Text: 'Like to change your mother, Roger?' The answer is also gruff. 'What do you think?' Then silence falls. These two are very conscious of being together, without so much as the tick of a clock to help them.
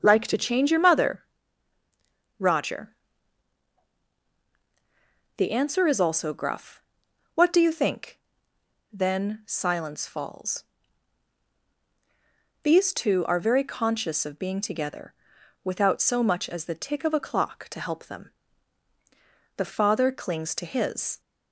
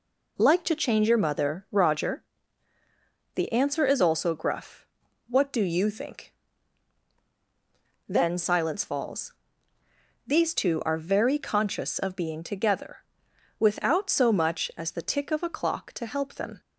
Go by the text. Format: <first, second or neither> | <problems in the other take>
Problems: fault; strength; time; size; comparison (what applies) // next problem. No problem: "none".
second | starts louder than the rest; until 1.0 s; 6.5 dB // goes on to say "The father clings to his"; from 19.5 s on; 1.6 s long